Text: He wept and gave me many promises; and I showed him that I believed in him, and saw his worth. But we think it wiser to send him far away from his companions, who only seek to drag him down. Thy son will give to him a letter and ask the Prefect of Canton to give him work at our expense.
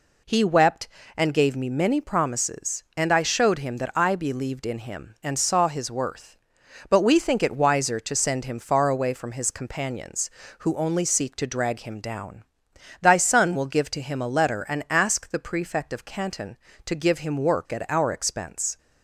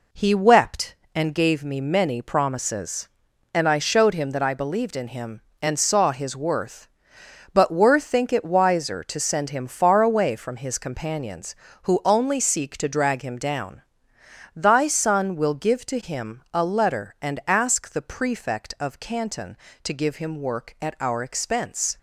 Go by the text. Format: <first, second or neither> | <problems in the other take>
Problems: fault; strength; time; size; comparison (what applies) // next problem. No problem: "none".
first | says "were" for "we"; at 7.7 s